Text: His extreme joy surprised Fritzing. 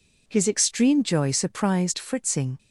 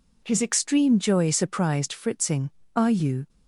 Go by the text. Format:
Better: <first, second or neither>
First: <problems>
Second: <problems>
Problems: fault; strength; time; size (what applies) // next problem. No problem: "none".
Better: first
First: none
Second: goes on to say "Are you"; from 2.7 s on; 0.54 s long